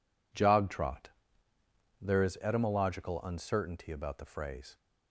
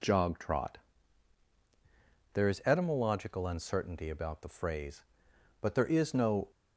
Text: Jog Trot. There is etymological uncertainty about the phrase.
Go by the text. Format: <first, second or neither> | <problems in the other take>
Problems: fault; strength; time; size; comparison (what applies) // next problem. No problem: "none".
first | goes on to say "But there is no"; noticeable; from 5.6 s on; 0.88 s long